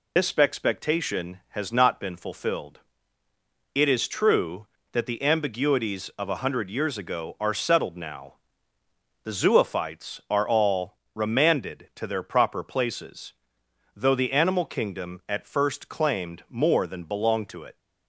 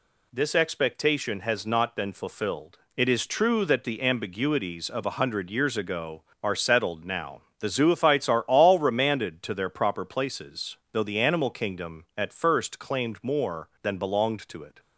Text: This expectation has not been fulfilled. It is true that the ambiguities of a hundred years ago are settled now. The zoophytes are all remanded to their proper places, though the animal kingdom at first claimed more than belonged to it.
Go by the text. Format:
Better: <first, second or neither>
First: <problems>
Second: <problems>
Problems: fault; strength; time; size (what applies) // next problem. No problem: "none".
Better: second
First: loses the start of "This"; at 0.1 s; 95 ms // pauses between "all" and "remanded"; slight; at 10.9 s; 0.18 s long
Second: none